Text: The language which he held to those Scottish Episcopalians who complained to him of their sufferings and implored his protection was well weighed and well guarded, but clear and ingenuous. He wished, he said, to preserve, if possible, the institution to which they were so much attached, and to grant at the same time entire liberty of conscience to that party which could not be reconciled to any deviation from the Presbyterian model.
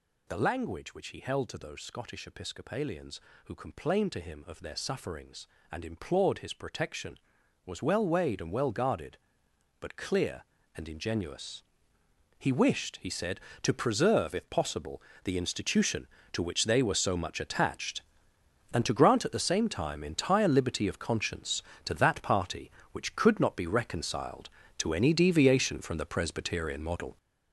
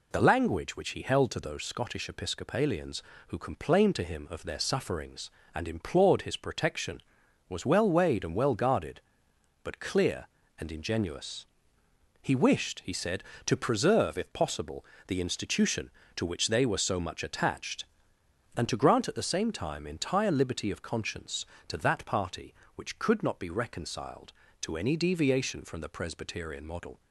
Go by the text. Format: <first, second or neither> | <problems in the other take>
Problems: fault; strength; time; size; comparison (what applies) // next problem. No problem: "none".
second | gets louder; strong; throughout; 7.5 dB